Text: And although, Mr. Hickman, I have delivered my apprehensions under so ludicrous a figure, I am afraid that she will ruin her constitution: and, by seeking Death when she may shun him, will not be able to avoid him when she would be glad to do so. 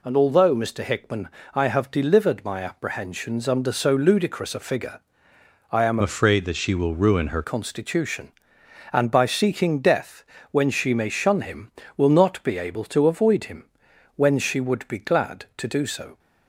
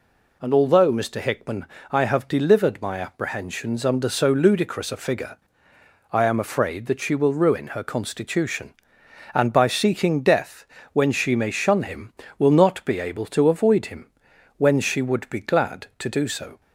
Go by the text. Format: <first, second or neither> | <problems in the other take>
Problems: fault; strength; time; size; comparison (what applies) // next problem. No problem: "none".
second | changes voice from "afraid" to "her"; from 6.0 to 7.4 s; 1.4 s long // pauses between "Death" and "when"; slight; at 10.2 s; 0.28 s long; slight in the second // pauses between "him" and "when"; noticeable; at 13.6 s; 0.52 s long; noticeable in the second